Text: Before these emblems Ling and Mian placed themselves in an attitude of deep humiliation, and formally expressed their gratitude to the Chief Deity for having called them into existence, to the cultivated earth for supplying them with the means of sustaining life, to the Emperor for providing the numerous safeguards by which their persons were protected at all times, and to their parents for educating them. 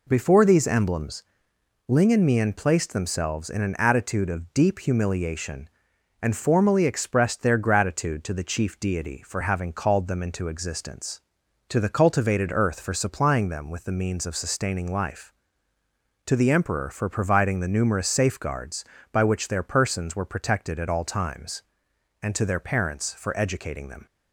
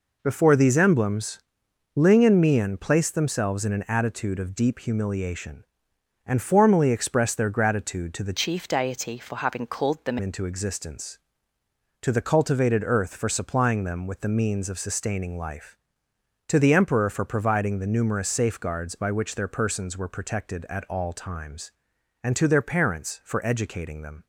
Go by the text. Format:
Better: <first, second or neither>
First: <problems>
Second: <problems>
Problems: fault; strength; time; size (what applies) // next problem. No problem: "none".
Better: first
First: pauses between "emblems" and "Ling"; noticeable; at 1.2 s; 0.64 s long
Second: pauses between "emblems" and "Ling"; noticeable; at 1.3 s; 0.56 s long // changes voice from "Chief" to "them"; from 8.3 to 10.1 s; 1.8 s long